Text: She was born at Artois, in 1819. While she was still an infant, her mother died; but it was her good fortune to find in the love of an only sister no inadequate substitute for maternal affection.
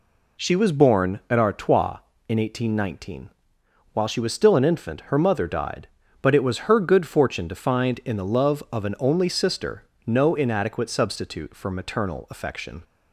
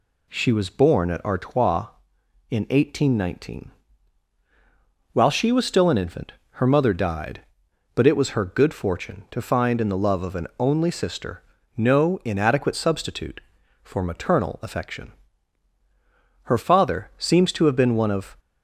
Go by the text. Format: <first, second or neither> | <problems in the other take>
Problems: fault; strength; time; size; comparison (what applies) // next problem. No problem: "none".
first | pauses between "sister" and "no"; slight; at 11.4 s; 0.34 s long; slight in the first // goes on to say "Her father seems to have been one of"; strong; from 16.4 s on; 1.9 s long